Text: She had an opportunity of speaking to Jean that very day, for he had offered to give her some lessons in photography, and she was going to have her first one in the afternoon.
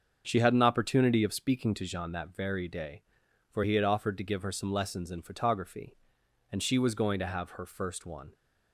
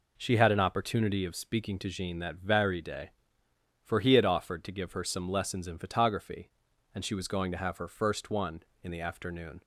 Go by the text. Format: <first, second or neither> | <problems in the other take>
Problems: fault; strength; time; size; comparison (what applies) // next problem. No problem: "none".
second | starts louder than the rest; until 1.2 s; 7 dB // stops before "in the afternoon"; at 8.3 s